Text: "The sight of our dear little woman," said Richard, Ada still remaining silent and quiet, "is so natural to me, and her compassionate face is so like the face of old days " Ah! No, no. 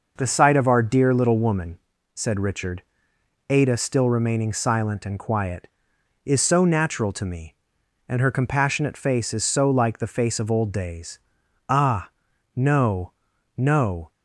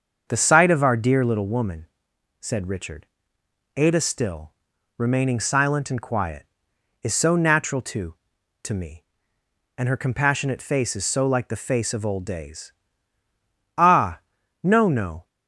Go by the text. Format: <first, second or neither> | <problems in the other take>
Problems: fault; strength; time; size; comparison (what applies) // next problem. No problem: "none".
first | starts louder than the rest; until 1.3 s; 6.5 dB // pauses between "still" and "remaining"; noticeable; at 4.5 s; 0.46 s long // says "to" twice; at 8.6 s